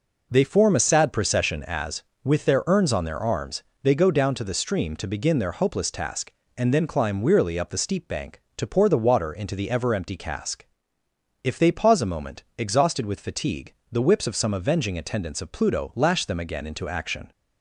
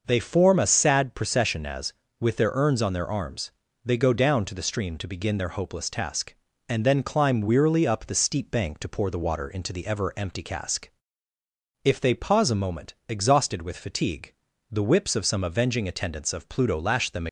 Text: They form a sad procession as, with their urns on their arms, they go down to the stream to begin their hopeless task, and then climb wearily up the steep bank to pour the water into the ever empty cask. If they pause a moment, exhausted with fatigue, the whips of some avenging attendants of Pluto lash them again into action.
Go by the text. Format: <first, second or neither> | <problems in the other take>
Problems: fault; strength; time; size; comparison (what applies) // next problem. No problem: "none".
first | starts louder than the rest; noticeable; until 1.0 s; 6 dB // stops before "again into action"; at 17.2 s